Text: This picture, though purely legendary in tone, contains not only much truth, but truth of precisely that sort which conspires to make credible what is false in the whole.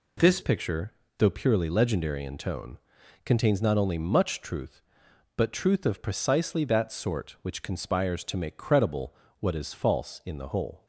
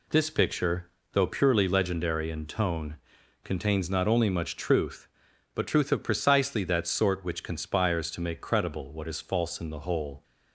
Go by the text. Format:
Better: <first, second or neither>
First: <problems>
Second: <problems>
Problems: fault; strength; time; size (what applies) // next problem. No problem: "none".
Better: second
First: changes voice at "picture"; from 0.4 s on; 10.4 s long // pauses between "credible" and "what"; slight; at 9.1 s; 0.26 s long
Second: none